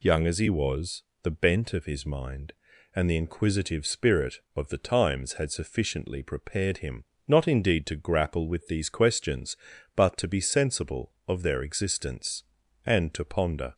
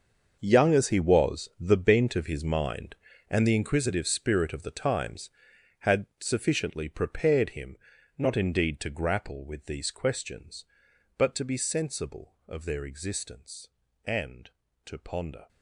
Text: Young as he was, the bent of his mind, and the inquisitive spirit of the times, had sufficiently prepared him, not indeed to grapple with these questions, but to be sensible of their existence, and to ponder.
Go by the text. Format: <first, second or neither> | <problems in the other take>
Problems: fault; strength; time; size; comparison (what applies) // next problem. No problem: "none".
first | gets quieter; strong; throughout; 15 dB